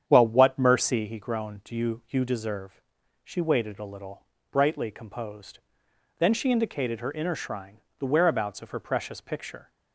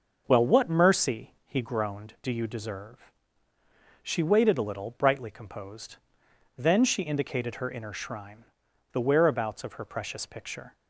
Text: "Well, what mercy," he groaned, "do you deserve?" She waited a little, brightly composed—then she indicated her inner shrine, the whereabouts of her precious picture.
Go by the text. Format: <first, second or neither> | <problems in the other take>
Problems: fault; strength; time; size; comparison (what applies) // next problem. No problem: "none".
second | starts louder than the rest; strong; until 1.0 s; 8.5 dB // says "you" twice; at 2.0 s